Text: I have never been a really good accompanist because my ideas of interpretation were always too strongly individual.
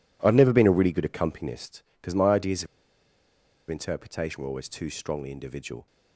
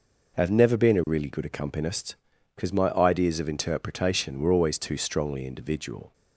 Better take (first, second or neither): second